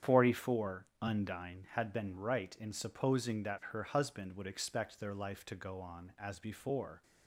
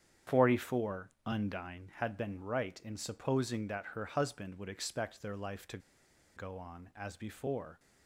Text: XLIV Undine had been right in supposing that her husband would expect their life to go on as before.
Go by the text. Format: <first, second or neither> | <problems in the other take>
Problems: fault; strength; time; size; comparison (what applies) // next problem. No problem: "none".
first | starts louder than the rest; strong; until 1.4 s; 8.5 dB; strong in the first // pauses between "to" and "go"; noticeable; at 5.7 s; 0.58 s long